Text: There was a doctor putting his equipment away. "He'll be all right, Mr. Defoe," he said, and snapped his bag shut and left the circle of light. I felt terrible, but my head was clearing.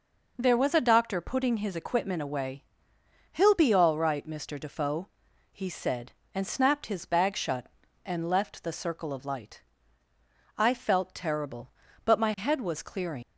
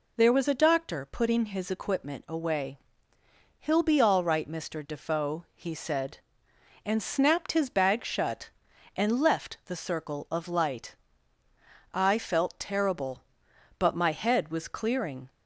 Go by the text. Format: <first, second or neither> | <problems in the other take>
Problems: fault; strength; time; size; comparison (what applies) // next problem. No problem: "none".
second | leaves "clearing" unfinished; at 13.2 s; 100 ms